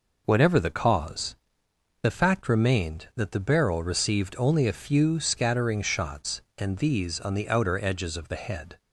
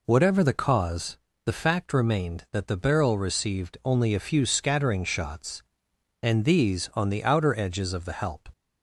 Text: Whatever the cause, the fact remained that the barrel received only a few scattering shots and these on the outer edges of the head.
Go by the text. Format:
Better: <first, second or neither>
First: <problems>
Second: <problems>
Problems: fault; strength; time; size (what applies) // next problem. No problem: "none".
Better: first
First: none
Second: says "help" for "head"; at 8.1 s